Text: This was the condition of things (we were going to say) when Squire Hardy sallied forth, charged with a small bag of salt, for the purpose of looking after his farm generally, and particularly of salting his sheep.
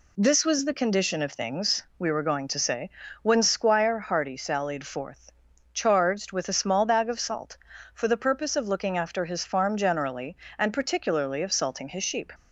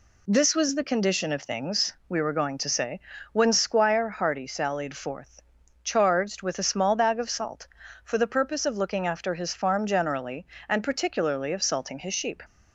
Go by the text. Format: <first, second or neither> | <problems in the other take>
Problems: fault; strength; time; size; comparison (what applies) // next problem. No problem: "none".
neither | none